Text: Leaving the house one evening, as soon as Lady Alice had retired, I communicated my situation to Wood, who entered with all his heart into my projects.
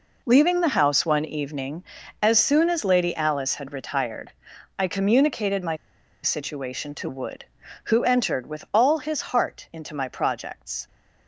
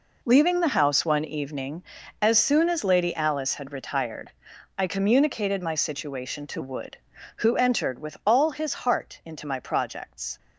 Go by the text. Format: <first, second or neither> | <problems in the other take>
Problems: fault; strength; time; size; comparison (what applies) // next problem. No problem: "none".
second | pauses between "my" and "situation"; noticeable; at 5.7 s; 0.49 s long